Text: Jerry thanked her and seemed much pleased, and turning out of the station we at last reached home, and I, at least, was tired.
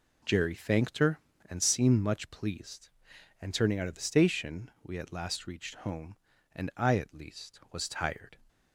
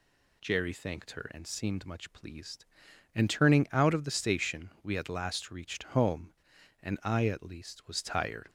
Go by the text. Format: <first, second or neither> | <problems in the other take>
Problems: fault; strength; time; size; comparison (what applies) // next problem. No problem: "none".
neither | none